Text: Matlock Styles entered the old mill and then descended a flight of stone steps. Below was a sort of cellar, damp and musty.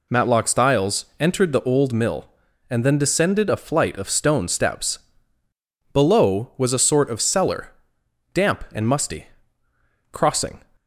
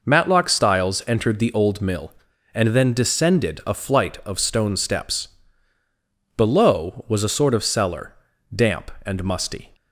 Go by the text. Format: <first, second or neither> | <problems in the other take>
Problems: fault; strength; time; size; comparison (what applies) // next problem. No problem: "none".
second | pauses between "Styles" and "entered"; slight; at 1.0 s; 0.16 s long // goes on to say "Crossing"; from 10.1 s on; 0.50 s long